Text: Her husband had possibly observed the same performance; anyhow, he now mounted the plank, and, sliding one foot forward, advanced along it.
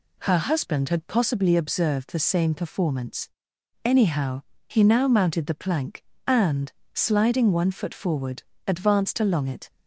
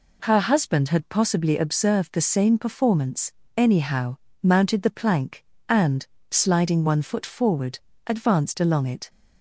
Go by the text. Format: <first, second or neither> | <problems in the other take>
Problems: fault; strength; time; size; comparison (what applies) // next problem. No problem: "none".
first | skips "he now"; at 4.2 s